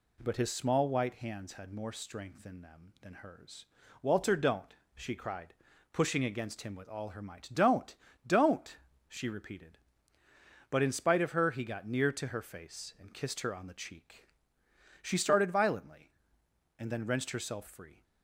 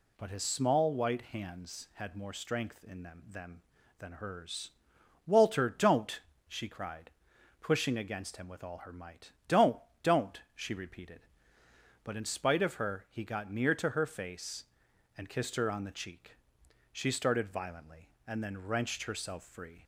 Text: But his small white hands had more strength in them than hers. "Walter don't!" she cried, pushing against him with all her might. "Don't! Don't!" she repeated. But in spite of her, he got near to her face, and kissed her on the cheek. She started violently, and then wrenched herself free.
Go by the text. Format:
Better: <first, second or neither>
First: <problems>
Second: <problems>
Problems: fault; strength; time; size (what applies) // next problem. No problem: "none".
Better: first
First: none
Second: says "them" twice; at 3.2 s